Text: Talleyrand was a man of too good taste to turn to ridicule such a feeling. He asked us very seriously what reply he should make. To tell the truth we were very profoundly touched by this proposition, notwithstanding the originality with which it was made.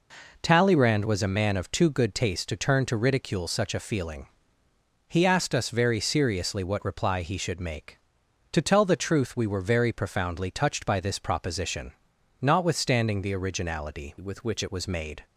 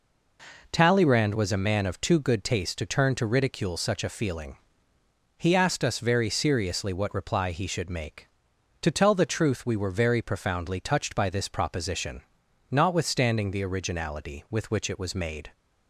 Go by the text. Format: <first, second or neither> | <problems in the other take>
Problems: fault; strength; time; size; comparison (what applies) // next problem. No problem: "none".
second | changes voice from "with" to "which"; from 14.1 to 14.6 s; 0.5 s long